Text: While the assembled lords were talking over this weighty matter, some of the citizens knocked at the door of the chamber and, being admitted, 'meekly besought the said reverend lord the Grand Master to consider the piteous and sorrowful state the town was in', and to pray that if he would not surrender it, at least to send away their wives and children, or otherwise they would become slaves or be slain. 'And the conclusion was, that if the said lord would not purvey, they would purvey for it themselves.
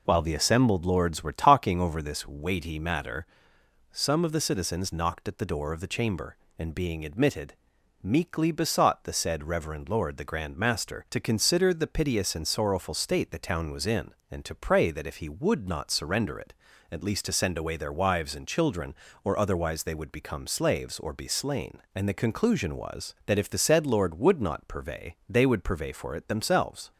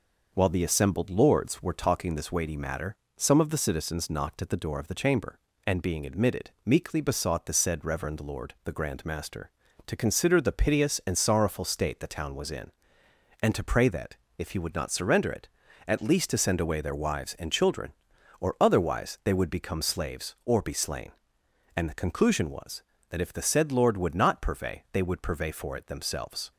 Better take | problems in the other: first | skips "over"; at 2.1 s // pauses between "that" and "if"; slight; at 14.1 s; 0.20 s long

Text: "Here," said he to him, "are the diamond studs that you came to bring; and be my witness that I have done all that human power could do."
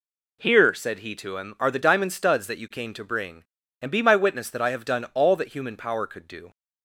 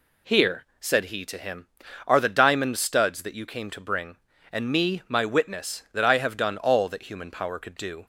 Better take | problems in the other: first | says "me" for "be"; at 4.7 s

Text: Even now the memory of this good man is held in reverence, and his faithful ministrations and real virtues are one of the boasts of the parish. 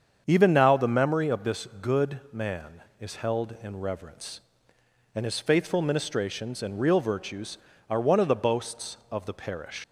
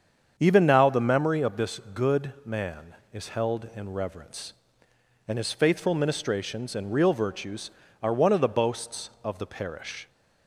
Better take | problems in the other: second | starts louder than the rest; strong; until 1.2 s; 7.5 dB; strong in the second // leaves "parish" unfinished; at 9.8 s; 120 ms

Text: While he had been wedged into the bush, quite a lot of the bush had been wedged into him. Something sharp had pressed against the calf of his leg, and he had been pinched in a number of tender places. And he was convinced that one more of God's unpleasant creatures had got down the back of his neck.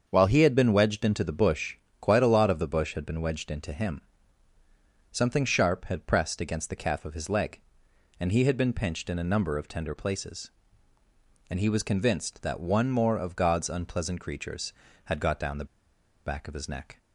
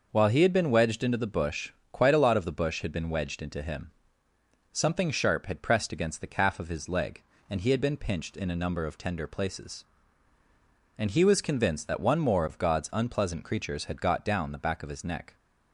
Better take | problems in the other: second | starts louder than the rest; until 1.0 s; 7 dB // pauses between "the" and "back"; noticeable; at 15.6 s; 0.61 s long

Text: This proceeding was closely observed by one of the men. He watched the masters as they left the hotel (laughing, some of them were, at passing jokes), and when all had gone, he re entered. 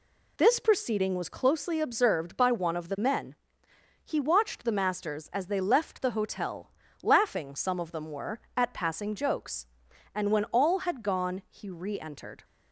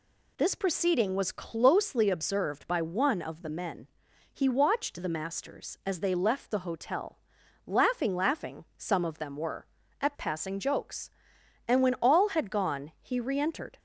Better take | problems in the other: first | says "laughing" twice; at 8.1 s

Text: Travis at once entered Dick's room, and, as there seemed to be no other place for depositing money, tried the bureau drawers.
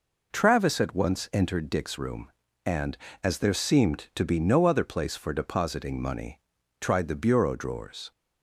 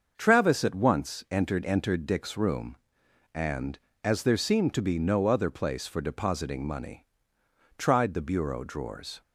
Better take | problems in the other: first | starts louder than the rest; until 1.1 s; 6.5 dB // says "entered" twice; at 1.6 s

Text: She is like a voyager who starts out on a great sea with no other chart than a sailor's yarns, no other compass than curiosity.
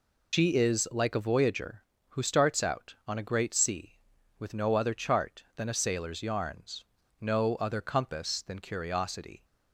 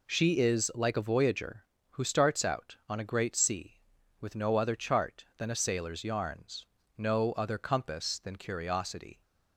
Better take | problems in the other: second | loses the start of "She"; at 0.3 s; 95 ms

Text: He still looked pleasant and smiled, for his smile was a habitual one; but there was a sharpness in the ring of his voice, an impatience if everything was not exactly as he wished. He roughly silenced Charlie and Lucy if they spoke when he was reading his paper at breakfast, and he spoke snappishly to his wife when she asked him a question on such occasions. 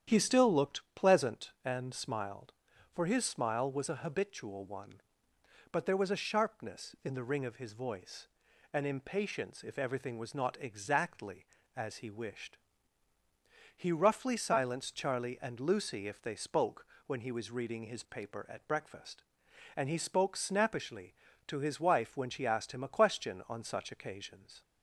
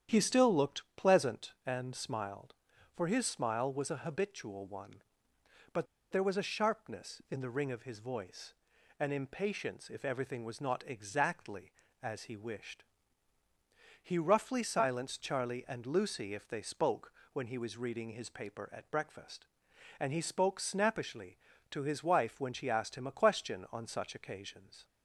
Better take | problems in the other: first | starts louder than the rest; strong; until 1.2 s; 9.5 dB; strong in the first // pauses between "but" and "there"; slight; at 5.8 s; 0.25 s long // pauses between "spoke" and "when"; slight; at 17.1 s; 0.18 s long; slight in the first

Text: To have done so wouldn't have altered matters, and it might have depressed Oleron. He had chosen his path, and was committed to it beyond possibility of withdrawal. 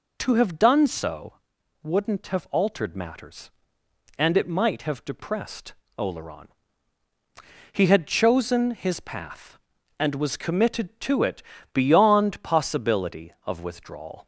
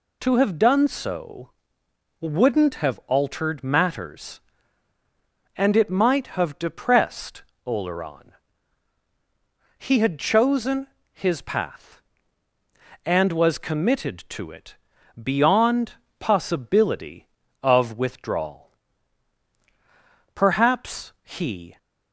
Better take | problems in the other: first | pauses between "so" and "wouldn't"; noticeable; at 1.5 s; 0.68 s long; noticeable in the first // pauses between "depressed" and "Oleron"; slight; at 7.4 s; 0.24 s long; slight in the first // pauses between "chosen" and "his"; slight; at 10.8 s; 0.26 s long // pauses between "it" and "beyond"; noticeable; at 14.7 s; 0.46 s long; slight in the first // pauses between "beyond" and "possibility"; slight; at 15.9 s; 0.26 s long // goes on to say "Perhaps he"; from 20.3 s on; 1.4 s long

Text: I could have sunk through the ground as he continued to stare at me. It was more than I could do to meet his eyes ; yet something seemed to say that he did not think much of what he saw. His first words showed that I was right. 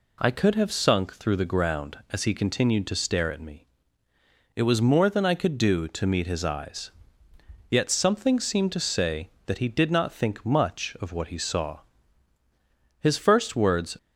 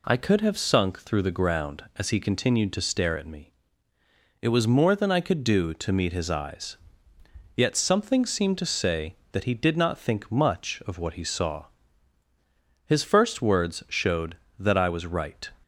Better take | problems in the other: second | stops before "showed that I was right"; at 13.9 s

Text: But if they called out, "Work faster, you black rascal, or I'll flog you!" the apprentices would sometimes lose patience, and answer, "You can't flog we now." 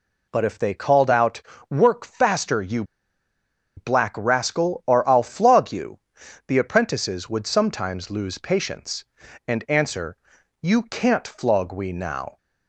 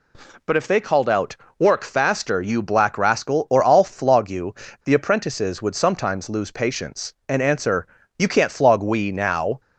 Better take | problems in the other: second | pauses between "you" and "black"; noticeable; at 2.8 s; 0.92 s long

